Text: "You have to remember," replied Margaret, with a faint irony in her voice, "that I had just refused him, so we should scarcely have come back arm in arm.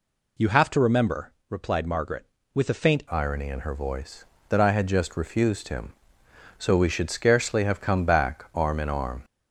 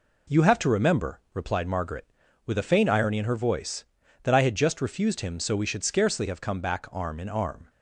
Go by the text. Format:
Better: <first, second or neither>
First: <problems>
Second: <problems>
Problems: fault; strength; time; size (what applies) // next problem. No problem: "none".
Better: second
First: changes voice at "irony"; from 3.1 s on; 6.1 s long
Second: none